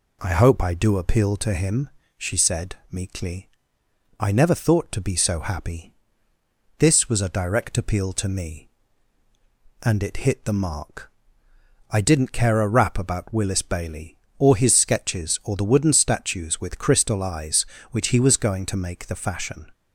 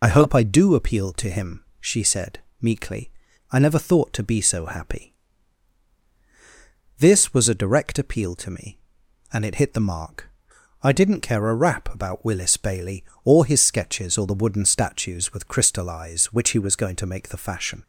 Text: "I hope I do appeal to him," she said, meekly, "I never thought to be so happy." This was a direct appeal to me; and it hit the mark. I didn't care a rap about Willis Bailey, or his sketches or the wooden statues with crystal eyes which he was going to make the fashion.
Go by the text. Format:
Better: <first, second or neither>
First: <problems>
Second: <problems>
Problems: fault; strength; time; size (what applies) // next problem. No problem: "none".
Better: first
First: none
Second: loses the start of "I"; at 0.0 s; 40 ms